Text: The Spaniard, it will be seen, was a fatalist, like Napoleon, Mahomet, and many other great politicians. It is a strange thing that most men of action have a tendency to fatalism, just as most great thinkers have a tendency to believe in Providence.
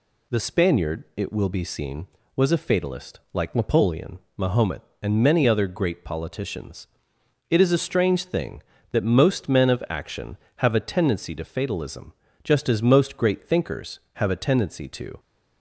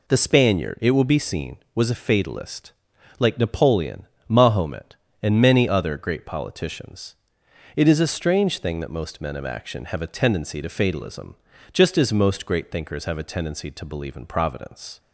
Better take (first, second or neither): second